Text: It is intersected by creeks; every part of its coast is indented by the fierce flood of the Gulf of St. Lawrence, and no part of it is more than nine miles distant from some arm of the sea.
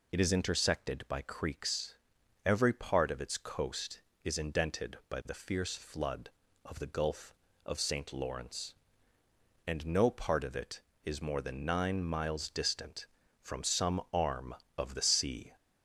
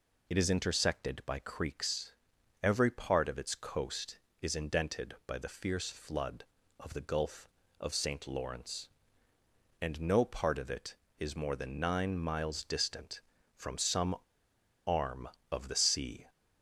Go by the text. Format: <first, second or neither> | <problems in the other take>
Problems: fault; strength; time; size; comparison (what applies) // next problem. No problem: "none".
first | pauses between "some" and "arm"; noticeable; at 14.1 s; 0.69 s long